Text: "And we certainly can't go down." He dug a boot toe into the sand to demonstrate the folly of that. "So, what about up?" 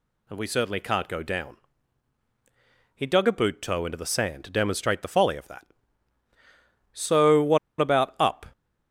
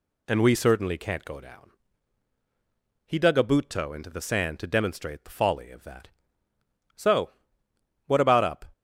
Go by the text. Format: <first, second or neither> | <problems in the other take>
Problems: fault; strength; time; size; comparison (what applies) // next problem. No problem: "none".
second | pauses between "what" and "about"; slight; at 7.5 s; 0.22 s long